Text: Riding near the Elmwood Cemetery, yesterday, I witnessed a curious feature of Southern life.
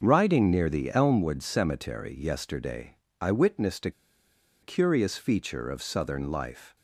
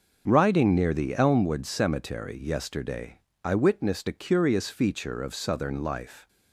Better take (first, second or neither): second